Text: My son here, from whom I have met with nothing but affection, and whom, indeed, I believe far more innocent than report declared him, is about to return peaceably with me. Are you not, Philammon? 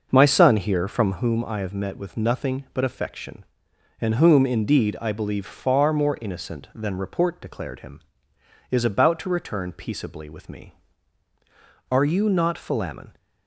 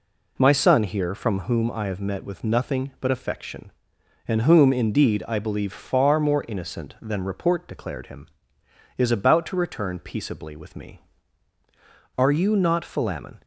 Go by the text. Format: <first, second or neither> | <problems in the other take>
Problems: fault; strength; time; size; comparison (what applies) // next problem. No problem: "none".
second | starts louder than the rest; noticeable; until 1.2 s; 6 dB